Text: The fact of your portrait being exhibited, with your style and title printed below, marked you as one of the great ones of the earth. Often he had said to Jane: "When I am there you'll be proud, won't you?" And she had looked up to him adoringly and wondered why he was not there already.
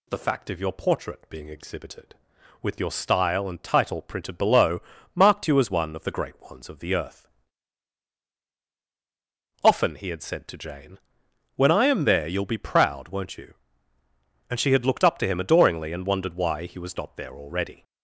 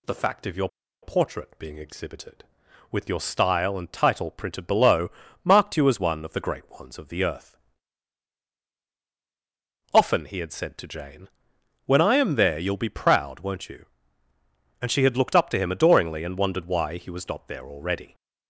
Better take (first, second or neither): first